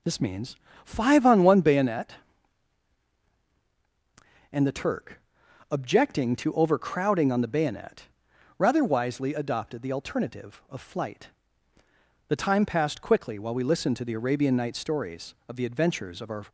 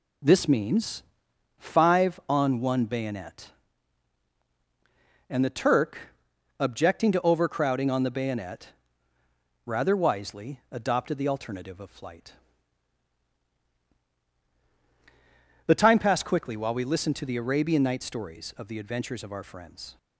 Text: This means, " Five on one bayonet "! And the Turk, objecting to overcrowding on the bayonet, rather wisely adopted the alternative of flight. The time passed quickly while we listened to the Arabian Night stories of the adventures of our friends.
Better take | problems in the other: second | stops before "friends"; at 16.4 s

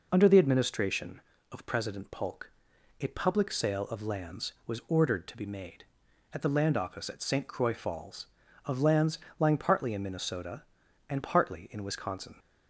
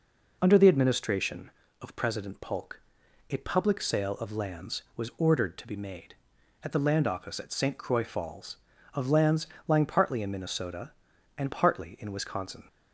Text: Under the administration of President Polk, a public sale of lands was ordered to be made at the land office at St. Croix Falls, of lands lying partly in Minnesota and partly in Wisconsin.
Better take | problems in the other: neither | pauses between "lands" and "lying"; slight; the same in both

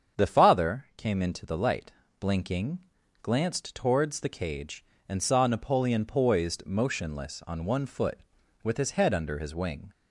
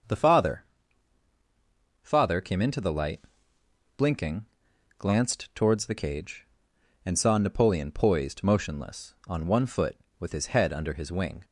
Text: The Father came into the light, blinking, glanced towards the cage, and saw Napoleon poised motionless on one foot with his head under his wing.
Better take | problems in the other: first | starts louder than the rest; until 2.4 s; 6.5 dB; strong in the first // says "Father" twice; at 2.0 s

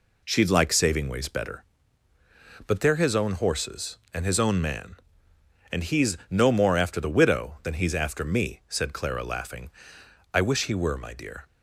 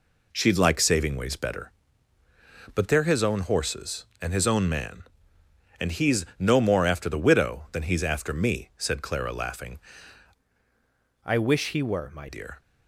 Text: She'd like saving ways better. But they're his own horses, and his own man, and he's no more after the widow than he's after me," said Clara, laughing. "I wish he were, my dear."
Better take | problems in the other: first | changes voice from "I" to "my"; from 11.2 to 12.2 s; 1.0 s long

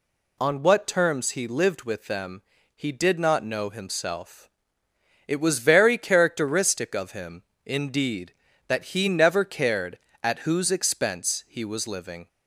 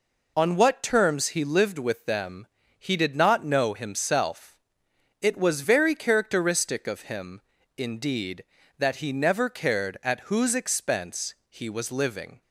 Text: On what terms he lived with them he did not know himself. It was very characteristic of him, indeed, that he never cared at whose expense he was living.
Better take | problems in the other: neither | pauses between "them" and "he"; slight; the same in both

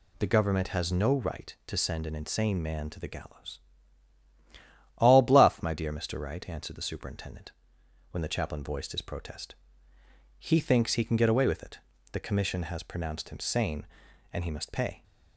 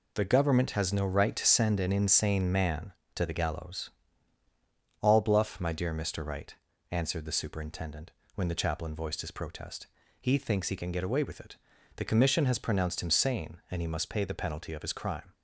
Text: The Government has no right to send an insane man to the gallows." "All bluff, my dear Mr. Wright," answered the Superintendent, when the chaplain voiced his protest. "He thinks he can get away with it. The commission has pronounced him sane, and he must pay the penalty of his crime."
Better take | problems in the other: second | stops before "the penalty of his crime"; at 15.0 s

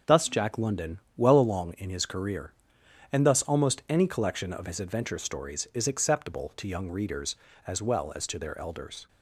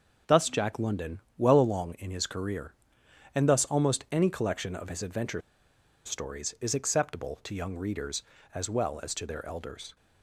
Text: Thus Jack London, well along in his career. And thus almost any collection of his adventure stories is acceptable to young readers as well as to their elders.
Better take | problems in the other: first | starts louder than the rest; until 1.4 s; 6.5 dB; also in the first // pauses between "adventure" and "stories"; noticeable; at 5.4 s; 0.64 s long

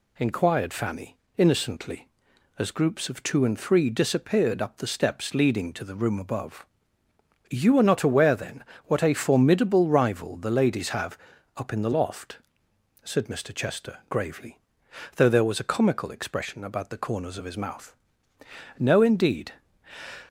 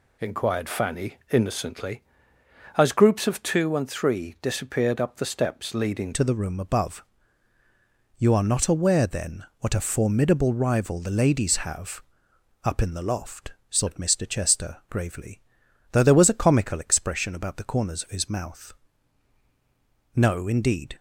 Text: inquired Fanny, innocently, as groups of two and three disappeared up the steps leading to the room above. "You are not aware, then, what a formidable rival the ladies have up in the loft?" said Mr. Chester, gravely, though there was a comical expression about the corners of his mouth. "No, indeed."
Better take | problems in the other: first | changes voice at "to"; from 6.1 s on; 14.8 s long // pauses between "have" and "up"; noticeable; at 12.0 s; 0.62 s long; also in the first

